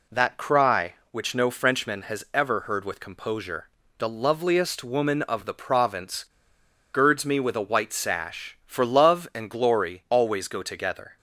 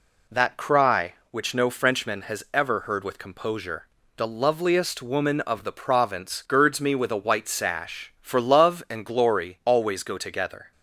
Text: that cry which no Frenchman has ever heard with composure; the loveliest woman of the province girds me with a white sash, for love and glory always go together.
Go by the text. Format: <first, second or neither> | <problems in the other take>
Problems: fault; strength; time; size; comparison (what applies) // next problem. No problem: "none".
second | pauses between "province" and "girds"; noticeable; at 6.2 s; 0.70 s long